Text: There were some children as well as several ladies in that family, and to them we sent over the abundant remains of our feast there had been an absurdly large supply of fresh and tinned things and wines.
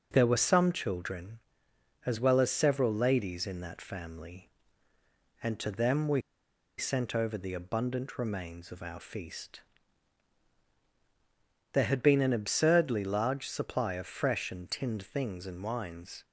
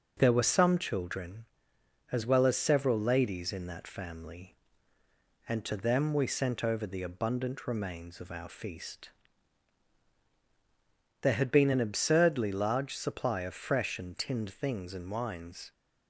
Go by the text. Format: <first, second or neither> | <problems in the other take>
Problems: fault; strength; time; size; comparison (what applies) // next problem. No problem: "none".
second | pauses between "we" and "sent"; noticeable; at 6.2 s; 0.57 s long // pauses between "feast" and "there"; strong; at 9.6 s; 2.1 s long; strong in the second